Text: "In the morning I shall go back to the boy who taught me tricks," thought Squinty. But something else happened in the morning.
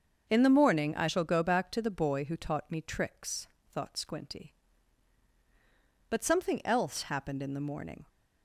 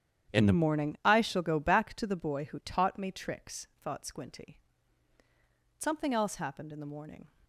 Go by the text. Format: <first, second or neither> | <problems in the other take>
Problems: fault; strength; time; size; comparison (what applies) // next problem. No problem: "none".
first | starts louder than the rest; strong; until 1.4 s; 9.5 dB; also in the first // skips "But"; at 5.2 s